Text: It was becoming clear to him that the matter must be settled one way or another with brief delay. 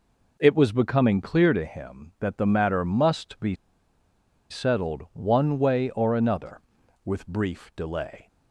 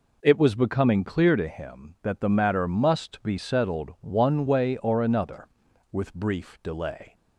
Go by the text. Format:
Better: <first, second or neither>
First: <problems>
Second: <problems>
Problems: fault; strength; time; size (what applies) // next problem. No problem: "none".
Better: second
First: pauses between "be" and "settled"; noticeable; at 3.5 s; 0.94 s long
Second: none